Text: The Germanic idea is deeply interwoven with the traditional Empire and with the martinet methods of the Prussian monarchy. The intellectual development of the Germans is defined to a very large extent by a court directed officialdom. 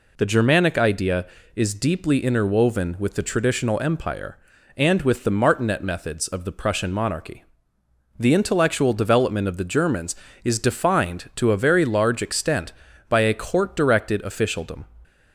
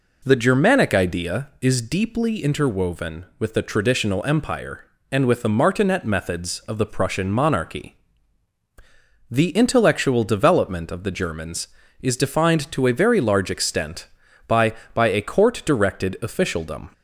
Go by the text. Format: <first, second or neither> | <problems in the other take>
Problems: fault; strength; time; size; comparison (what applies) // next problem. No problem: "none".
first | says "by" twice; at 14.9 s